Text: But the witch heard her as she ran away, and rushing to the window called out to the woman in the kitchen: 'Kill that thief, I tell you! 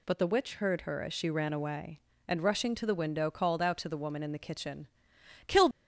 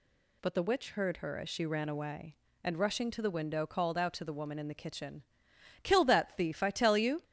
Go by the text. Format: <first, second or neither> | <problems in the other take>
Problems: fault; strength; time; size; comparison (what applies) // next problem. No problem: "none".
second | stops before "that thief I tell you"; at 5.7 s